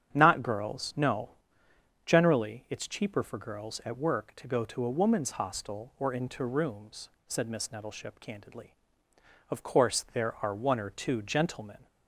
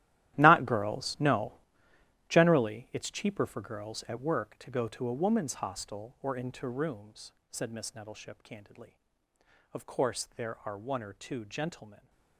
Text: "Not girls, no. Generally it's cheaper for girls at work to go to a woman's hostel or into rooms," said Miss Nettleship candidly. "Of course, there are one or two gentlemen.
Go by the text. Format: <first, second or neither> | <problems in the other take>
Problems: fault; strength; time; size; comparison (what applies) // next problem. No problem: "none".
first | gets quieter; strong; throughout; 16 dB // starts louder than the rest; strong; until 1.4 s; 13.5 dB; strong in the first